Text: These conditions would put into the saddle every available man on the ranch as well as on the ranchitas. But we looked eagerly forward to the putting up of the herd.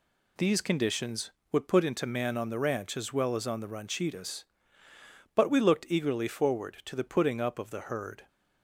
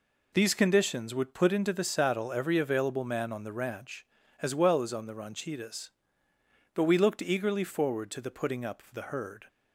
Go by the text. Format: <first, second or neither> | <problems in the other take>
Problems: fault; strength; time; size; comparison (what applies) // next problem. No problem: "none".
second | skips "the saddle every available"; at 2.0 s